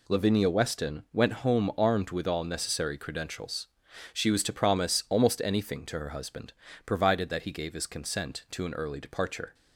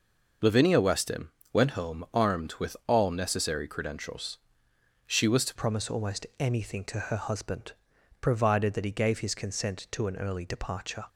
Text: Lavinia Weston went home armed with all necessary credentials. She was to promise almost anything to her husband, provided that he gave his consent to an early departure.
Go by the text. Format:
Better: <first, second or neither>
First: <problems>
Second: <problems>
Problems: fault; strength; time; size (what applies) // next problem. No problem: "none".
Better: first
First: none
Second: pauses between "Weston" and "went"; slight; at 1.2 s; 0.24 s long // changes voice at "promise"; from 5.5 s on; 5.5 s long